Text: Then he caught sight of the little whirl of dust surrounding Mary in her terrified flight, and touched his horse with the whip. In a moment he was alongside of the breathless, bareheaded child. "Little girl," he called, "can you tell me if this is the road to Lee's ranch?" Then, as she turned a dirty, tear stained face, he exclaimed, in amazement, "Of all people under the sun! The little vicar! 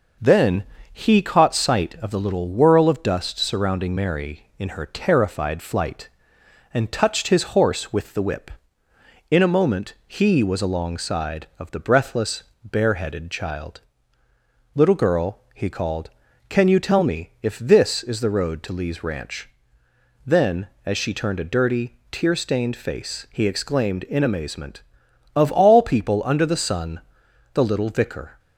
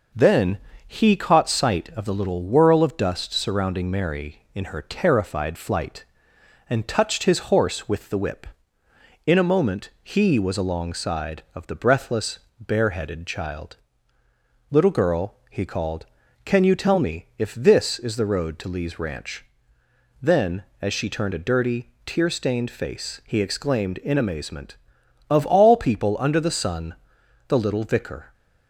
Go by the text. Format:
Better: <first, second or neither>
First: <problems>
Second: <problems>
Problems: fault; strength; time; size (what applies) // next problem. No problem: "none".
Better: neither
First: pauses between "Then" and "he"; slight; at 0.6 s; 0.28 s long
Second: pauses between "Then" and "he"; slight; at 0.5 s; 0.28 s long